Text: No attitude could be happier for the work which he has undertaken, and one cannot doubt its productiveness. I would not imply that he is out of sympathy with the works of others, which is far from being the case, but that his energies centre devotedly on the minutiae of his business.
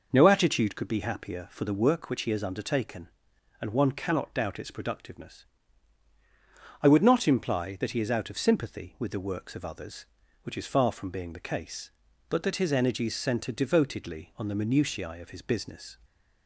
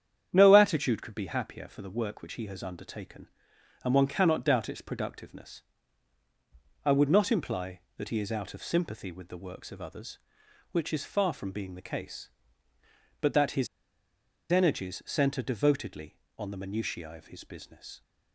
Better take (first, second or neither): first